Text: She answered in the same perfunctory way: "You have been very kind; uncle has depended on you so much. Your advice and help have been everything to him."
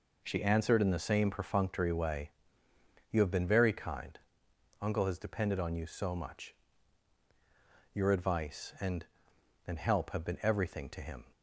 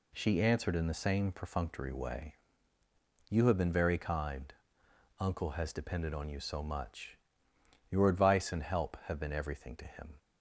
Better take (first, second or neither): second